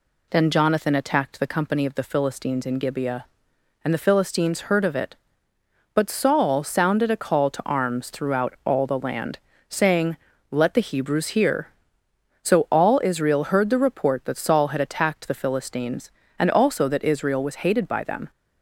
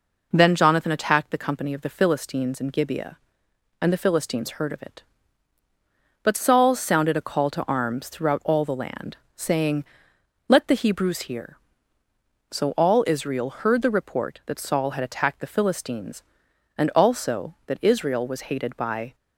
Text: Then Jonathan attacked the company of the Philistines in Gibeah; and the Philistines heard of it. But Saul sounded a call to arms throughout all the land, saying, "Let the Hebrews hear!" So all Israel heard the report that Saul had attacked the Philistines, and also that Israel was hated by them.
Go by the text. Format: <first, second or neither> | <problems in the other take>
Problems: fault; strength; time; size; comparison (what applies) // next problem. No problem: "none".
first | stops before "them"; at 19.1 s